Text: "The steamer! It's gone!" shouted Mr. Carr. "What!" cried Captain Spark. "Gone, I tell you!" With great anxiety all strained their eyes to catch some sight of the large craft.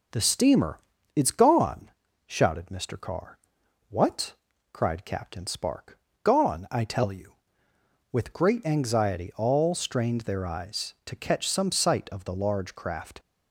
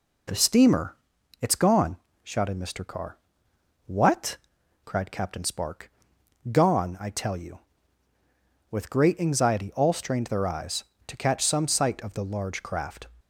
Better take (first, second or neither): neither